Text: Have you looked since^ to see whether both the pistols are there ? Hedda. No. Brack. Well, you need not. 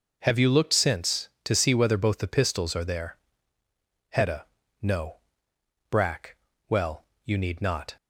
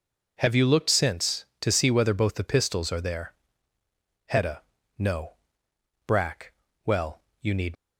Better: first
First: none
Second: stops before "not"; at 7.7 s

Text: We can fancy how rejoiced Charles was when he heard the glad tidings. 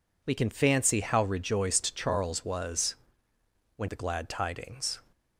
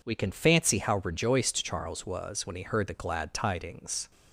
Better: second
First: pauses between "was" and "when"; noticeable; at 2.9 s; 0.80 s long // skips "he heard"; at 3.8 s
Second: none

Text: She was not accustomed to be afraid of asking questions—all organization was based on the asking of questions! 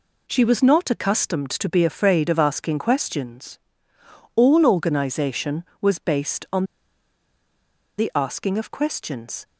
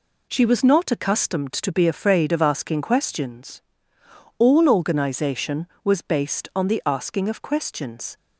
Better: second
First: pauses between "on" and "the"; strong; at 6.6 s; 1.3 s long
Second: none

